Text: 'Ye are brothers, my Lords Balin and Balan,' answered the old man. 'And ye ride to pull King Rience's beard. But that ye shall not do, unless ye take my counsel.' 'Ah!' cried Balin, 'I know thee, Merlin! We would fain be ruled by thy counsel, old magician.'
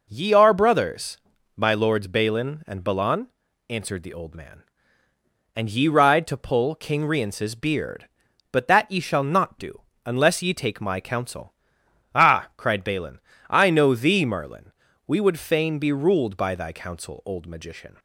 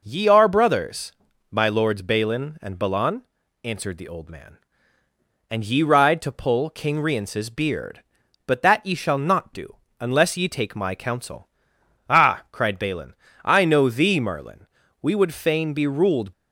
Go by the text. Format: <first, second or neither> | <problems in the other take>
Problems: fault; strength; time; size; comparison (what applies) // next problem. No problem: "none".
first | stops before "by thy counsel old magician"; at 16.3 s